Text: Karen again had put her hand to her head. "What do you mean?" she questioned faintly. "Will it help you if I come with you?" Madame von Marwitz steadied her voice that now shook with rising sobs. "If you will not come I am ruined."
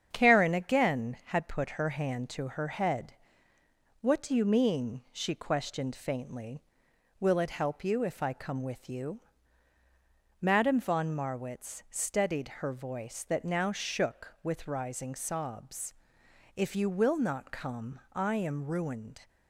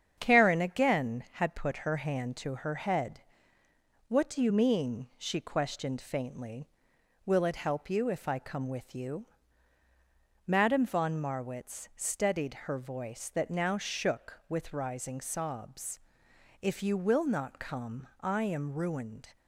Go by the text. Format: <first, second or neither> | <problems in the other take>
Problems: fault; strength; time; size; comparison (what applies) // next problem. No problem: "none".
neither | starts louder than the rest; strong; the same in both